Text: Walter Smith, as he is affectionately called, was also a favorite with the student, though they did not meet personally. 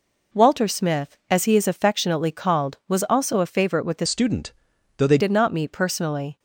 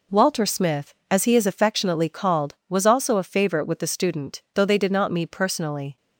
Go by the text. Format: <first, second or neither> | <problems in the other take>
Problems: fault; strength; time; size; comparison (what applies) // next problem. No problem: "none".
second | changes voice from "student" to "they"; from 4.0 to 5.1 s; 1.1 s long